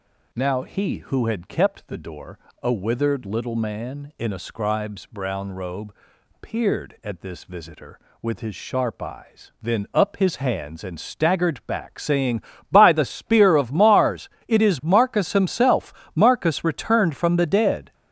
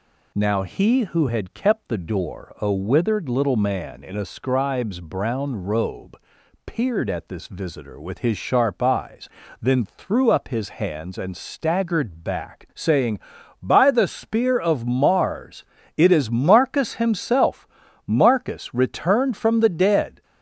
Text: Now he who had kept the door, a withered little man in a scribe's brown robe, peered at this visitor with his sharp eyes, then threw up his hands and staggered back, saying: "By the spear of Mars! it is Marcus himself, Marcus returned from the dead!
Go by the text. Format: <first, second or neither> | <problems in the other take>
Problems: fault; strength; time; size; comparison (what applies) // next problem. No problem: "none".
second | skips "threw"; at 9.8 s